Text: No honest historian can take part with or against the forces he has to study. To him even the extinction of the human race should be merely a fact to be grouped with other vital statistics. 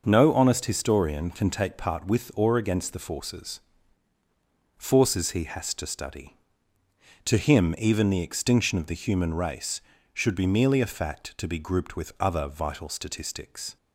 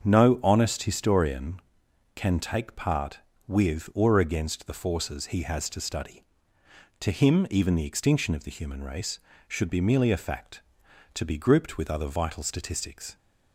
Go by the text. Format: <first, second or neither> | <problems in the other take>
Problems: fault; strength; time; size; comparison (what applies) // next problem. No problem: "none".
second | starts louder than the rest; noticeable; until 1.0 s; 6 dB; also in the second // says "forces" twice; at 4.7 s